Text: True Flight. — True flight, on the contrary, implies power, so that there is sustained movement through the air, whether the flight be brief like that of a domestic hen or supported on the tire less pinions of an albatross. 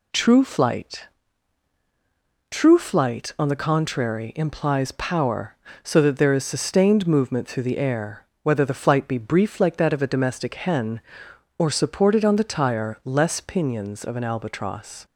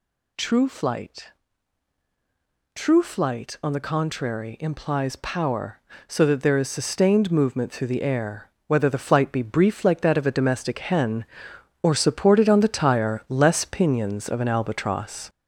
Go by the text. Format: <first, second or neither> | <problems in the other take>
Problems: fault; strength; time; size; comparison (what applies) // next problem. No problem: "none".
first | gets louder; noticeable; throughout; 4.5 dB